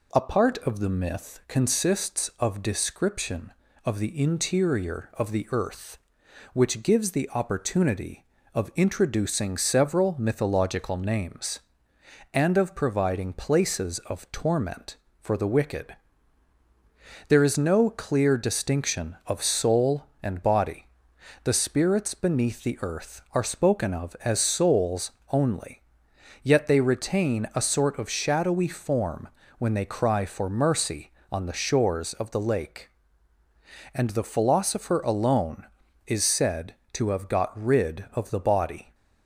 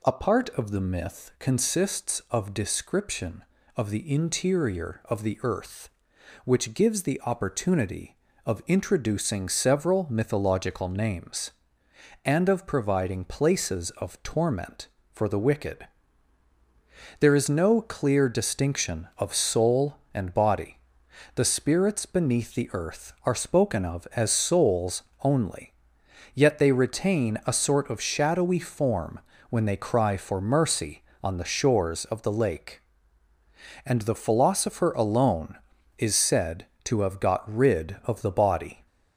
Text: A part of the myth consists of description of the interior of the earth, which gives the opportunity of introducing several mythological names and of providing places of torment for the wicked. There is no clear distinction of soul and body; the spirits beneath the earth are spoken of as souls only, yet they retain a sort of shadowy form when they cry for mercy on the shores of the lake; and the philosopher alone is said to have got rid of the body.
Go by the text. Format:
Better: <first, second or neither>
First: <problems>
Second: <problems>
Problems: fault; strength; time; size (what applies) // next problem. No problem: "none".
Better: first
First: pauses between "souls" and "only"; slight; at 25.1 s; 0.18 s long // pauses between "form" and "when"; slight; at 29.2 s; 0.30 s long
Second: gets louder; throughout; 3.5 dB // pauses between "souls" and "only"; slight; at 25.0 s; 0.18 s long // pauses between "form" and "when"; slight; at 29.1 s; 0.30 s long